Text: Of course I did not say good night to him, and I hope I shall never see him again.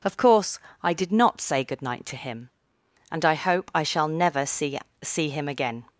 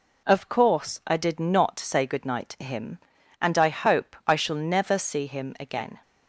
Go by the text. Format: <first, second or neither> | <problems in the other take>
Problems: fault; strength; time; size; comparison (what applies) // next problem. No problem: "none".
second | pauses between "course" and "I"; slight; at 0.5 s; 0.22 s long // says "see" twice; at 5.0 s